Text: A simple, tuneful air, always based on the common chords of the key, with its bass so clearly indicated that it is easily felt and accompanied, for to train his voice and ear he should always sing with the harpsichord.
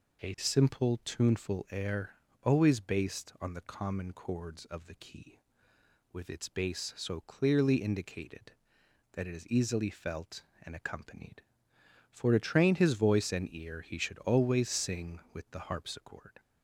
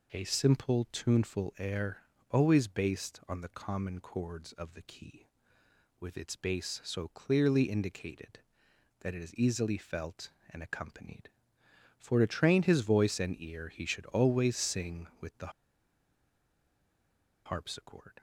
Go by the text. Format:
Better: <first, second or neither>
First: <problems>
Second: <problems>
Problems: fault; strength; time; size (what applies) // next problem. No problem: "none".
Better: first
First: none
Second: pauses between "the" and "harpsichord"; strong; at 15.5 s; 1.9 s long